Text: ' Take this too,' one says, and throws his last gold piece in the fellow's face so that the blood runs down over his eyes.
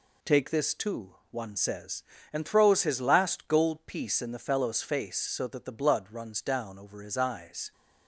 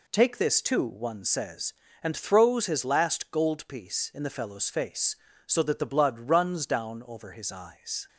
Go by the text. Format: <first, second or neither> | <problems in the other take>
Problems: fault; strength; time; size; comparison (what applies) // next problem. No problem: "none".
neither | none